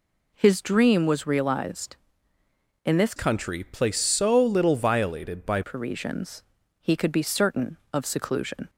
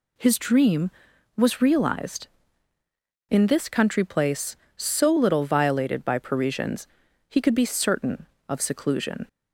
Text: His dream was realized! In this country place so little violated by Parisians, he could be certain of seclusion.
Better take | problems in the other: second | changes voice from "country" to "by"; from 3.1 to 5.6 s; 2.5 s long

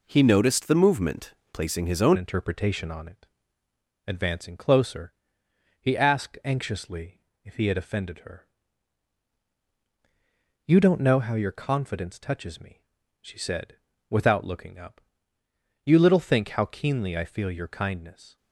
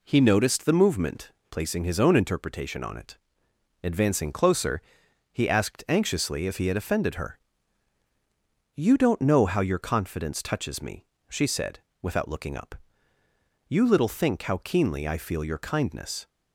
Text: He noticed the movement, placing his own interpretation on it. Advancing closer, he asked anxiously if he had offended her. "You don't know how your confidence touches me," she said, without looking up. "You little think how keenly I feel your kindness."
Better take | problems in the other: second | changes voice at "interpretation"; from 2.1 s on; 16.2 s long // pauses between "anxiously" and "if"; slight; at 7.2 s; 0.24 s long

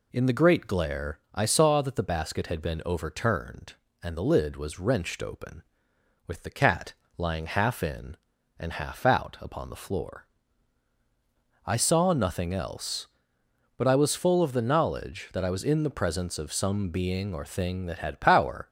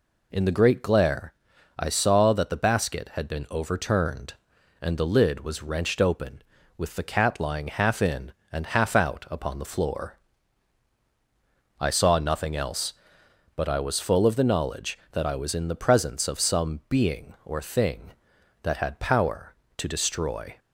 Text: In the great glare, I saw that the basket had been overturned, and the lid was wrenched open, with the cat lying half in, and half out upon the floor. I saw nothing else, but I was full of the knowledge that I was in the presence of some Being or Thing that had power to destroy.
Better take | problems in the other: second | pauses between "cat" and "lying"; slight; at 6.9 s; 0.22 s long // stops before "to destroy"; at 18.6 s

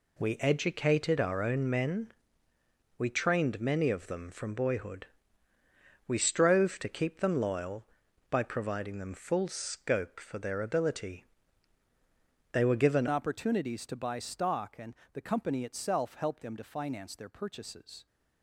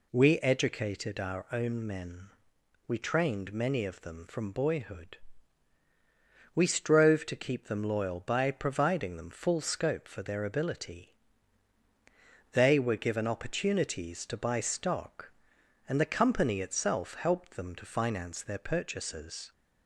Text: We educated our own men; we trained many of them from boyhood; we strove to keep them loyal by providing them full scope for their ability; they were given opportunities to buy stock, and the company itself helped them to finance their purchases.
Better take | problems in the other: second | changes voice at "opportunities"; from 13.0 s on; 5.0 s long // pauses between "and" and "the"; slight; at 14.9 s; 0.18 s long

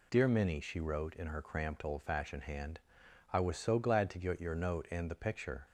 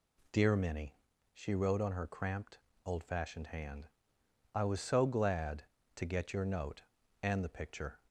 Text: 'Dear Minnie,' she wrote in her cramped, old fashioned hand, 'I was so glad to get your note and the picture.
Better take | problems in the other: first | says "on" for "in"; at 1.8 s

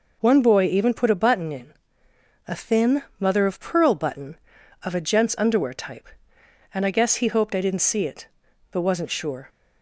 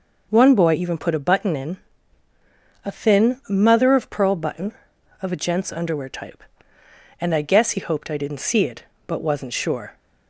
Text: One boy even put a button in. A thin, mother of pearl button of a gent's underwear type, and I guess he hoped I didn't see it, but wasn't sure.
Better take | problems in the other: neither | none

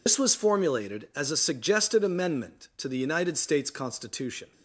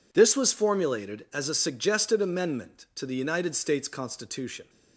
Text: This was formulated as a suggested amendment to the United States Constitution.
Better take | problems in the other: second | loses the start of "This"; at 0.0 s; 105 ms

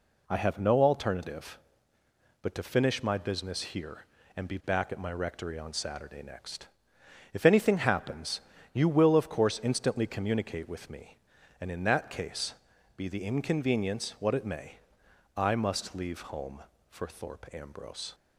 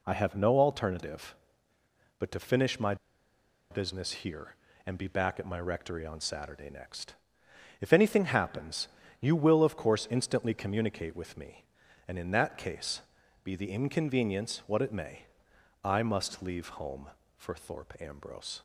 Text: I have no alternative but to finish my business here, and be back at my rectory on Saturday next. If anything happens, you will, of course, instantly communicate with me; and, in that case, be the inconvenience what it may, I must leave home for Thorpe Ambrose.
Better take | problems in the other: first | pauses between "my" and "business"; noticeable; at 2.9 s; 0.76 s long

